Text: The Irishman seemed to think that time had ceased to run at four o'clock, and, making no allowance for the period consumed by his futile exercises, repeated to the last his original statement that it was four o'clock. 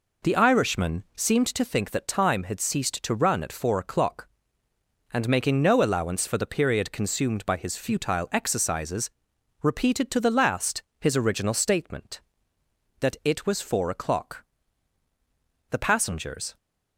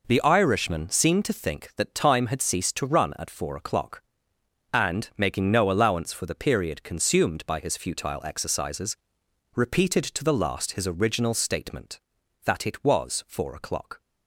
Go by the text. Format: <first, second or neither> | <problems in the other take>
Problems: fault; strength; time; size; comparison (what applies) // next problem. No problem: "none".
second | pauses between "last" and "his"; slight; at 10.8 s; 0.18 s long // goes on to say "The passengers"; noticeable; from 15.7 s on; 0.86 s long